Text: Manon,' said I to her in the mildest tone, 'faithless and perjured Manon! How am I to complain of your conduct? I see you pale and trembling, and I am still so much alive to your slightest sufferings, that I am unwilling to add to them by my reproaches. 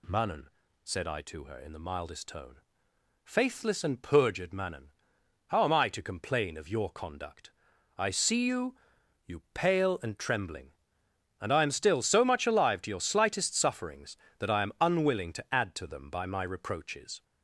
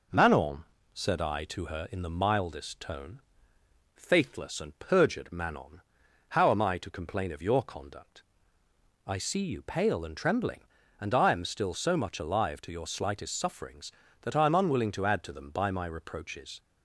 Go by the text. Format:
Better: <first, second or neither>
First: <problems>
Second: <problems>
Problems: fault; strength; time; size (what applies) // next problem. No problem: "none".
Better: second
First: says "you" twice; at 9.2 s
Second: none